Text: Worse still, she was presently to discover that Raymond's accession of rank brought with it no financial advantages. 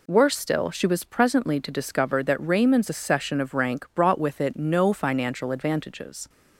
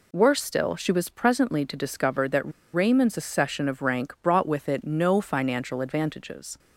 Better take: first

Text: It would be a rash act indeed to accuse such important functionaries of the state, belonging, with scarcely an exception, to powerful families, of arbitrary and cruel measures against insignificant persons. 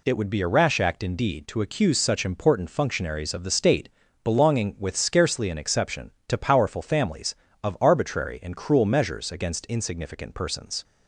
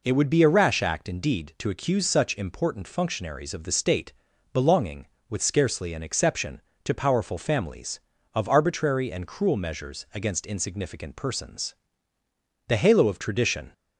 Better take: first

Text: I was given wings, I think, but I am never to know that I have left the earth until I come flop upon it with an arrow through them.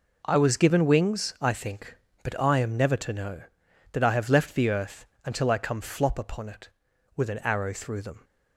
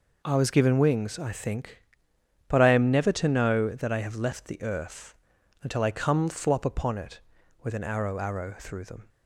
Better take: first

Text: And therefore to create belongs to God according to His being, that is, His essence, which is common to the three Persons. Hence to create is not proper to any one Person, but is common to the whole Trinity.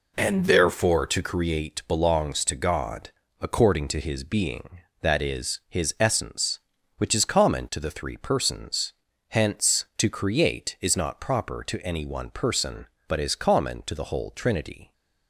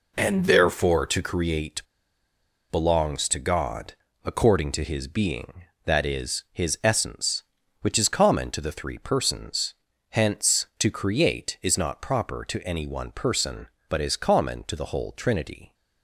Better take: first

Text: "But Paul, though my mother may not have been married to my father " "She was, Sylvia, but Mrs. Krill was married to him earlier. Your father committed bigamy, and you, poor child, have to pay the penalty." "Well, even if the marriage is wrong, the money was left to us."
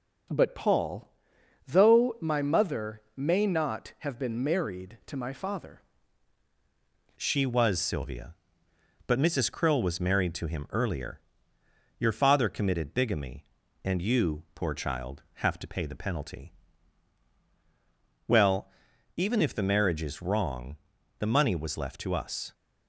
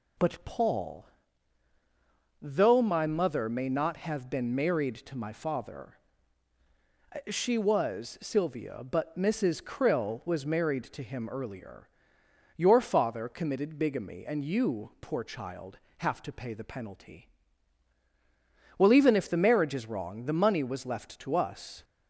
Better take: second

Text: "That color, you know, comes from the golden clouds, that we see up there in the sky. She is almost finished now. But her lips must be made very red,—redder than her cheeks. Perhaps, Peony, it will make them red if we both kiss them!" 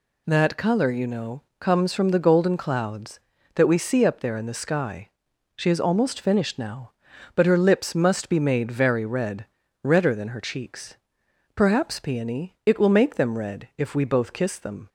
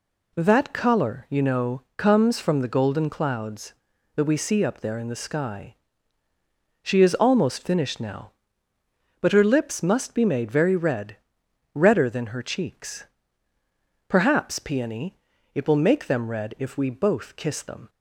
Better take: neither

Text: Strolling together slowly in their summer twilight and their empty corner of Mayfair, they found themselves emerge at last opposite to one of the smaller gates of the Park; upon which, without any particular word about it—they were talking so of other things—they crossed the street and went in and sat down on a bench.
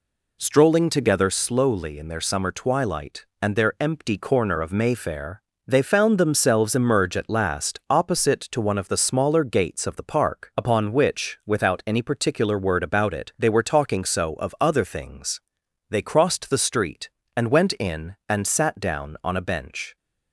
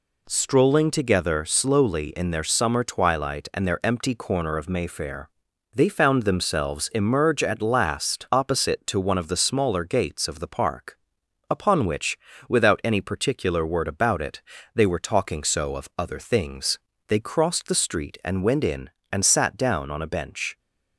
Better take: neither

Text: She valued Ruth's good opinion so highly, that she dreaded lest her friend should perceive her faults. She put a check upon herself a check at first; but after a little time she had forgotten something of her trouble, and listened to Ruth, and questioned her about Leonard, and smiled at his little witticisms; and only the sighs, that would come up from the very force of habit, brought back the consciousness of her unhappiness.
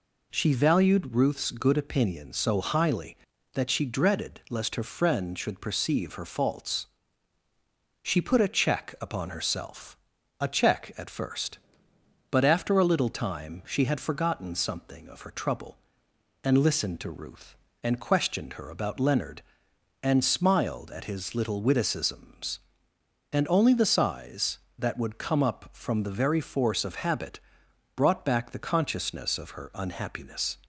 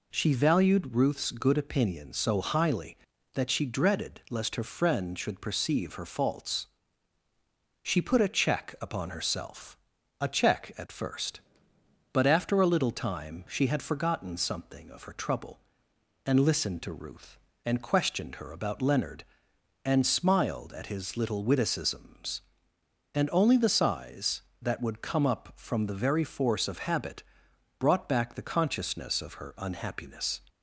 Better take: neither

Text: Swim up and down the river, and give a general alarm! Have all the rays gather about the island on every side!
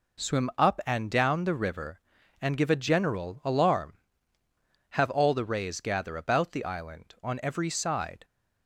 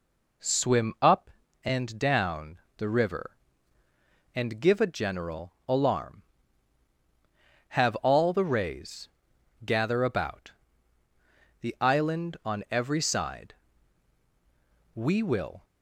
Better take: first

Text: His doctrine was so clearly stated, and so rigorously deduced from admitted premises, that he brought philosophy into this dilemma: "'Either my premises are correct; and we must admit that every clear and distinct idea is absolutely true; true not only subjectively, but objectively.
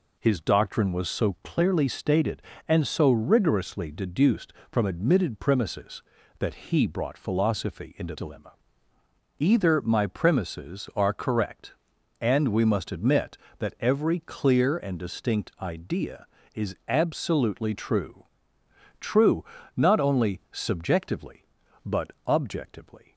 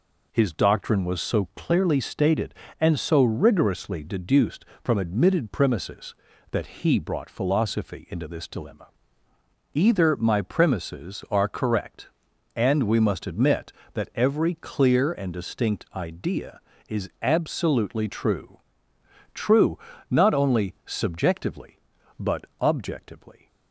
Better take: second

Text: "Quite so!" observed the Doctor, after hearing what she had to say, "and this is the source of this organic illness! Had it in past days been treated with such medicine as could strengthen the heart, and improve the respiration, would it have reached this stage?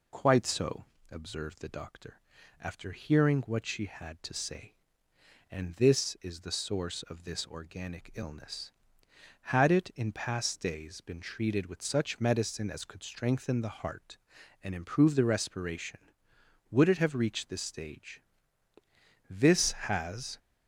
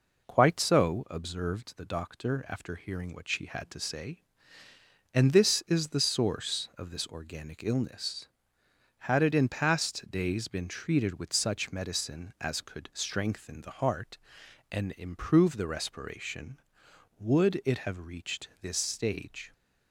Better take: second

